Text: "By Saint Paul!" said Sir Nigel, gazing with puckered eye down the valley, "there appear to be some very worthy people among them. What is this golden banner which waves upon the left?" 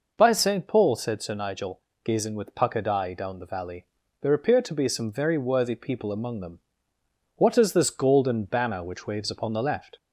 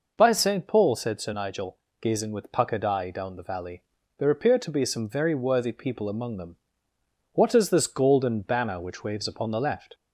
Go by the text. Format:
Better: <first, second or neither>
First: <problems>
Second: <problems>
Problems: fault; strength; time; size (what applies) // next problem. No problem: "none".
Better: neither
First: none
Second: none